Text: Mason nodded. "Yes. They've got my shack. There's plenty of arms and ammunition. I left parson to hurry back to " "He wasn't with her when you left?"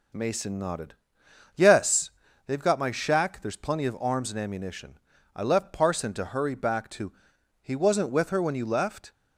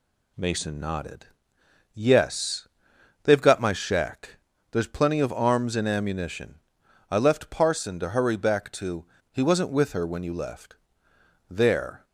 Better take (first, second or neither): first